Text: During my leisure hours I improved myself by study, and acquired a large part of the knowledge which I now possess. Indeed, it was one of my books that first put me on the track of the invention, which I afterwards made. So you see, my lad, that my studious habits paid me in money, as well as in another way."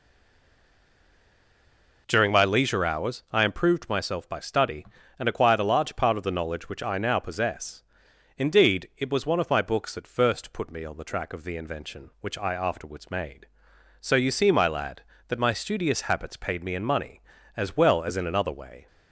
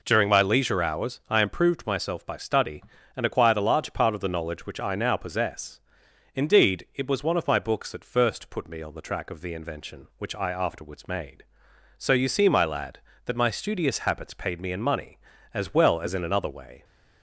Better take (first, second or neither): second